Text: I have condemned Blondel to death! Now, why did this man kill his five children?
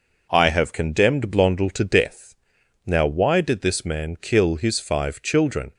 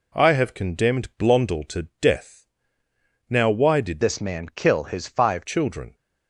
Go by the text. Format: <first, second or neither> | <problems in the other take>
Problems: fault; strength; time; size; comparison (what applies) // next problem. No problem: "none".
first | changes voice from "this" to "five"; from 4.0 to 5.4 s; 1.4 s long